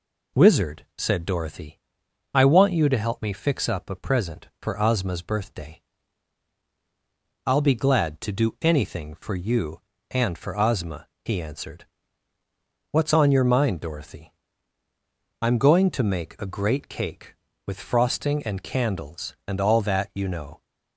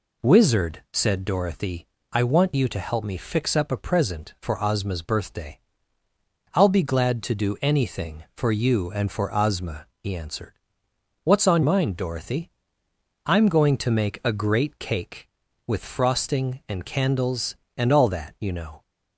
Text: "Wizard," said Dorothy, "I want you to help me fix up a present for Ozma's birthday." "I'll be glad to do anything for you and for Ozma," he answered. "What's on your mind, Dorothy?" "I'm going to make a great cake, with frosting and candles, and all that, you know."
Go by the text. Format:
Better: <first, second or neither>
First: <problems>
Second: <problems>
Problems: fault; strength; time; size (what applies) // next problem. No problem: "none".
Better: first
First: none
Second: skips "your"; at 11.6 s